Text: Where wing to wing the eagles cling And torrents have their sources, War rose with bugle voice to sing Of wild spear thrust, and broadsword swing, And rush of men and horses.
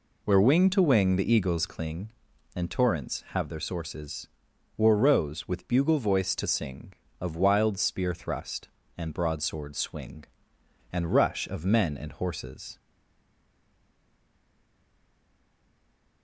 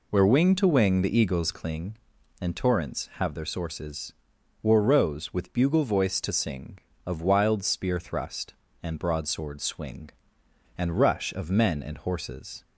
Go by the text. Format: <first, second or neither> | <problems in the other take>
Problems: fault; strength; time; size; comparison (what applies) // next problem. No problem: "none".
second | stays silent after the last word; strong; from 12.7 s on; 3.5 s long